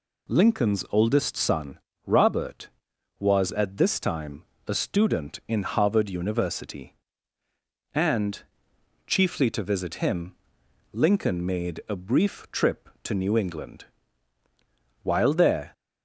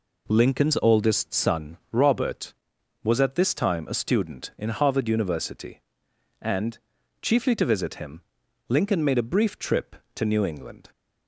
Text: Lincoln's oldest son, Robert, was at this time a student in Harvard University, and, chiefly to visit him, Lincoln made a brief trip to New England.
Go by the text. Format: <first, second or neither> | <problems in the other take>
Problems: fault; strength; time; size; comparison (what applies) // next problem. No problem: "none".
second | pauses between "time" and "a"; slight; at 4.4 s; 0.24 s long // goes on to say "While there"; noticeable; from 15.0 s on; 0.70 s long